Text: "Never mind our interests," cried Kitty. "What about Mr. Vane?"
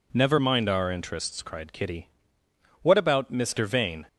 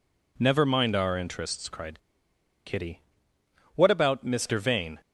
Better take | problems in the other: first | pauses between "cried" and "Kitty"; noticeable; at 1.9 s; 0.67 s long

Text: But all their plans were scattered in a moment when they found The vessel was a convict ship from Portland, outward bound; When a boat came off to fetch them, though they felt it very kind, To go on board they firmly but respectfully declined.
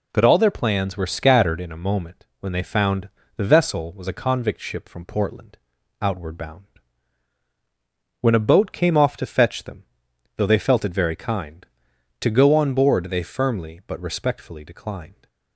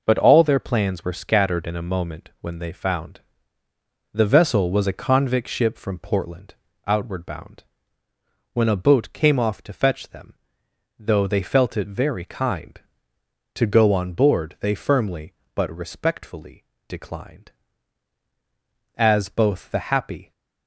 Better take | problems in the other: first | pauses between "found" and "The"; noticeable; at 3.1 s; 0.94 s long; slight in the first // pauses between "respectfully" and "declined"; slight; at 16.6 s; 0.24 s long // goes on to say "As both the happy"; from 18.9 s on; 1.3 s long

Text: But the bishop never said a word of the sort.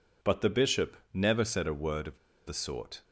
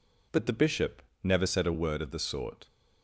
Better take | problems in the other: second | pauses between "bishop" and "never"; slight; at 0.9 s; 0.16 s long; slight in the second // pauses between "of" and "the"; slight; at 2.1 s; 0.28 s long

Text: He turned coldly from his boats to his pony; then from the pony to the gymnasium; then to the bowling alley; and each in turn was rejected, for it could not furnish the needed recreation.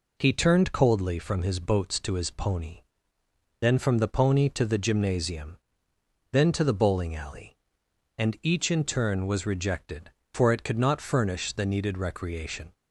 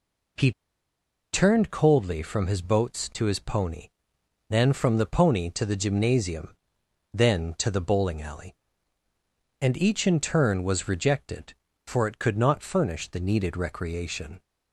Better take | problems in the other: first | pauses between "He" and "turned"; noticeable; at 0.5 s; 0.80 s long

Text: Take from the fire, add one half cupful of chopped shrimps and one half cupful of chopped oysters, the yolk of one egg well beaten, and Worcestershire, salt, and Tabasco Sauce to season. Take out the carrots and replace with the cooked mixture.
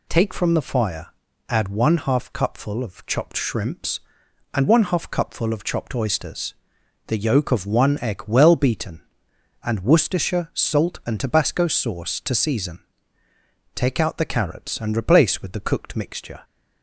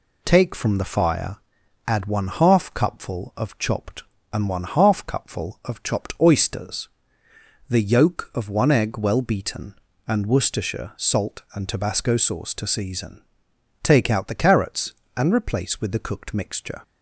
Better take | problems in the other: first | skips "shrimps"; at 4.1 s

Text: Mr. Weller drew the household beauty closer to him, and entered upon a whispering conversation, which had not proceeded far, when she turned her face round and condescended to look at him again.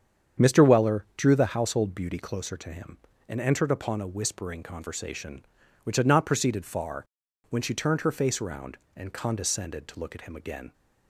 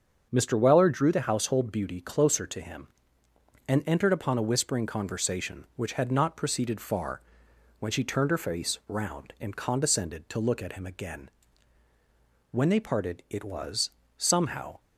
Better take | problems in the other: first | starts louder than the rest; until 1.3 s; 7 dB; strong in the first // goes on to say "When they parted it was somehow"; strong; from 12.4 s on; 2.3 s long

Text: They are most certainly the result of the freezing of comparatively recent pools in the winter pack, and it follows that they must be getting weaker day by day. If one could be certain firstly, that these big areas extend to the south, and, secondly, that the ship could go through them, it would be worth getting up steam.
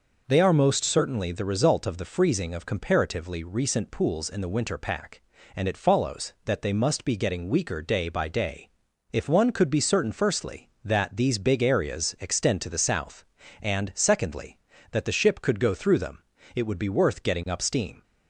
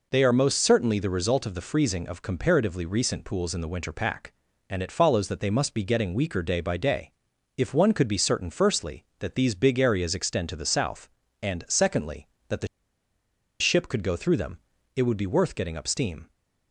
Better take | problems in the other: first | pauses between "the" and "ship"; noticeable; at 12.6 s; 0.93 s long

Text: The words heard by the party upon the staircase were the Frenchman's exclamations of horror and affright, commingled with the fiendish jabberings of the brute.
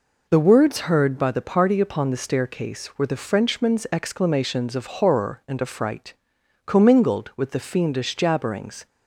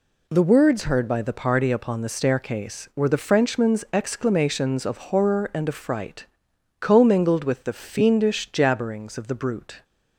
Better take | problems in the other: second | stops before "of the brute"; at 8.8 s

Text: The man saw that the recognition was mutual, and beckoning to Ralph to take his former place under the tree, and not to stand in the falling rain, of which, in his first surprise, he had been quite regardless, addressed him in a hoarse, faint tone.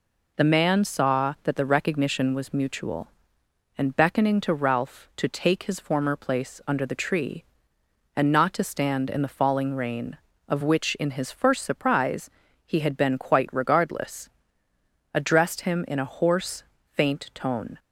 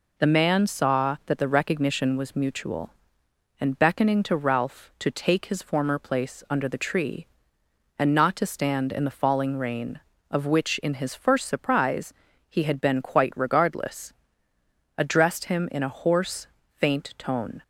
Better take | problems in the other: neither | none

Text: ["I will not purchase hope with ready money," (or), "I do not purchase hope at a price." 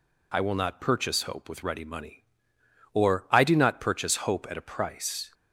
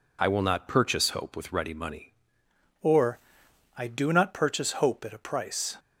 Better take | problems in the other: first | changes voice at "or"; from 2.7 s on; 3.0 s long

